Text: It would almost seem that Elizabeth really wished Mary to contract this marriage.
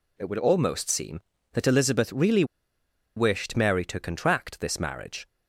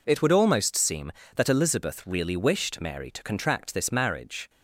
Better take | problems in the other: second | pauses between "really" and "wished"; noticeable; at 2.4 s; 0.72 s long

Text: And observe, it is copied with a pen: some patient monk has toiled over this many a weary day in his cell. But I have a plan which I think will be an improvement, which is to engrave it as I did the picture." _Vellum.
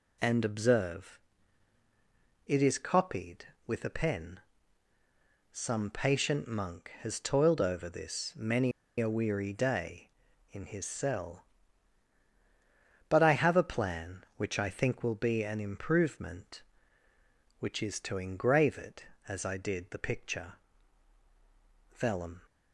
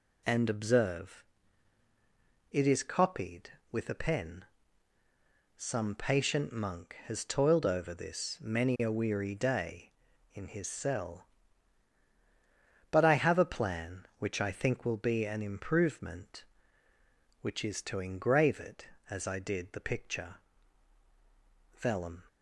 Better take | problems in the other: second | pauses between "many" and "a"; slight; at 8.7 s; 0.29 s long

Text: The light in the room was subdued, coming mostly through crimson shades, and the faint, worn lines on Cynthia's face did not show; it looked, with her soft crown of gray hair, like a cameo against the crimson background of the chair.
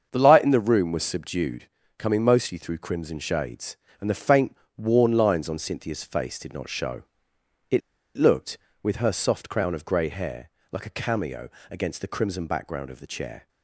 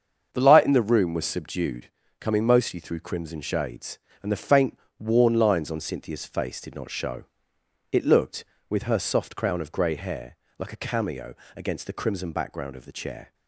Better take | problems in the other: second | starts louder than the rest; until 1.1 s; 7 dB; also in the second // pauses between "it" and "looked"; at 7.8 s; 0.37 s long // pauses between "cameo" and "against"; slight; at 11.5 s; 0.20 s long; slight in the second

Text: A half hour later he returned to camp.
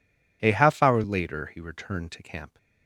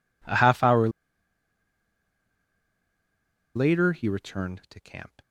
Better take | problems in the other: first | pauses between "hour" and "later"; strong; at 0.8 s; 2.6 s long

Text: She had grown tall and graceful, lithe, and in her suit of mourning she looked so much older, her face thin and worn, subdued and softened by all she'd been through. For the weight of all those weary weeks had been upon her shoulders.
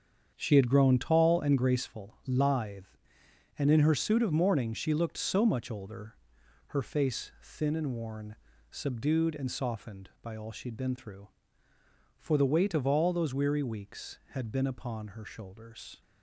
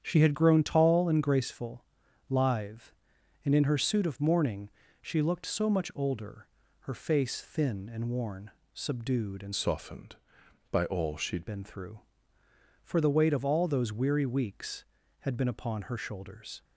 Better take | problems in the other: first | starts louder than the rest; strong; until 1.0 s; 8.5 dB; strong in the first // pauses between "mourning" and "she"; slight; at 4.6 s; 0.32 s long // changes voice from "softened" to "she'd"; from 9.5 to 11.4 s; 1.9 s long

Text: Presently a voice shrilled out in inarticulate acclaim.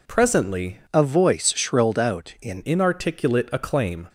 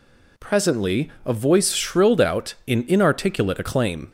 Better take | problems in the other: second | changes voice from "a" to "in"; from 0.9 to 2.6 s; 1.7 s long

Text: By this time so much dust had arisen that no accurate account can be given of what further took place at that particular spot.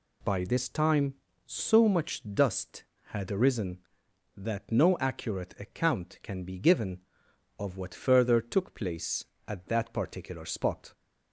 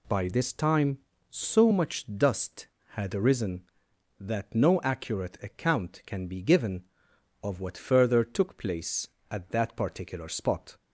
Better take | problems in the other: neither | none

